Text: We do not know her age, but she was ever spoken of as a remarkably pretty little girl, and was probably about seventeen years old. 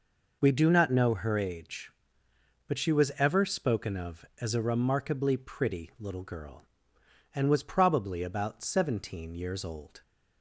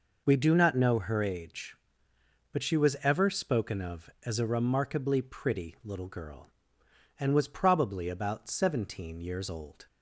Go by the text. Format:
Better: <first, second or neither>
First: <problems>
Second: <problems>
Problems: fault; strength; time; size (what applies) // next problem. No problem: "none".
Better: neither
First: none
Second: none